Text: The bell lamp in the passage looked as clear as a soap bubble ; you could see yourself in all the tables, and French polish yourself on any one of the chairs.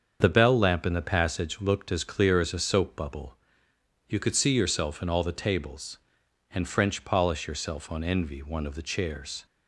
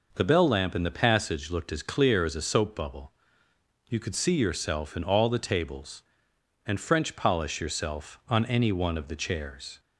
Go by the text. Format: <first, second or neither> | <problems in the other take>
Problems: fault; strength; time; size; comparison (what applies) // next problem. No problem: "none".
second | starts louder than the rest; strong; until 1.2 s; 7 dB // says "envy" for "any"; at 8.0 s